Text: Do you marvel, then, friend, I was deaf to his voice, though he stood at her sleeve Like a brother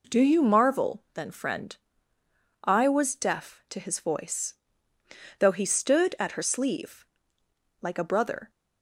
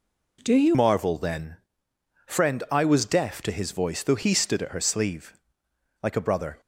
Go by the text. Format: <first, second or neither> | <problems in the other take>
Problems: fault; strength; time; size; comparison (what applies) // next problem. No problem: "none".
first | changes voice at "marvel"; from 0.7 s on; 5.9 s long // pauses between "sleeve" and "Like"; noticeable; at 5.3 s; 0.68 s long; noticeable in the first